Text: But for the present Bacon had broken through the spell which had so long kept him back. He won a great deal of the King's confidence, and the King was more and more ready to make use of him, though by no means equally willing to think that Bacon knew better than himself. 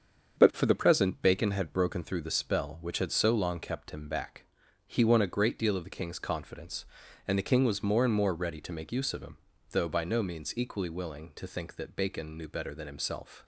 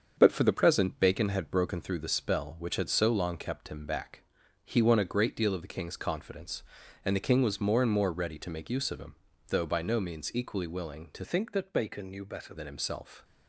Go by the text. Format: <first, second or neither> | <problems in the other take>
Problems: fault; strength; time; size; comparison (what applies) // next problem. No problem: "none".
first | starts louder than the rest; until 1.1 s; 7 dB; also in the first // changes voice from "think" to "better"; from 11.2 to 12.5 s; 1.3 s long